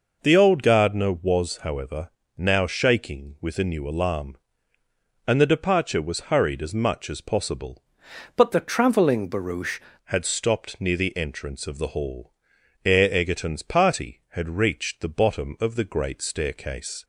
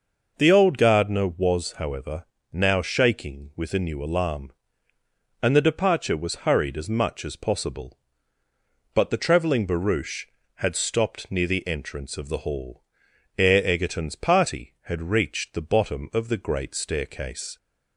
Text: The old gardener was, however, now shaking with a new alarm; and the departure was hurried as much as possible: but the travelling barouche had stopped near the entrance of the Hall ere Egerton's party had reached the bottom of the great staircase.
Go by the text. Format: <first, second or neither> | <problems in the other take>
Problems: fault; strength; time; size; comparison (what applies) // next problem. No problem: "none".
second | changes voice from "but" to "barouche"; from 8.3 to 9.8 s; 1.5 s long // pauses between "Hall" and "ere"; noticeable; at 12.3 s; 0.54 s long; noticeable in the second